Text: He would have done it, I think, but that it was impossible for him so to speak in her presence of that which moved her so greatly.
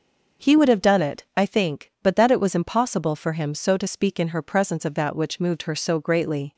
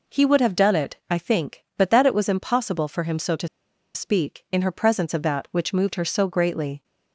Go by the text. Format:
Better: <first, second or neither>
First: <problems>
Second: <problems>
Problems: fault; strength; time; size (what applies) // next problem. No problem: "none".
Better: first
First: none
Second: pauses between "to" and "speak"; noticeable; at 3.4 s; 0.47 s long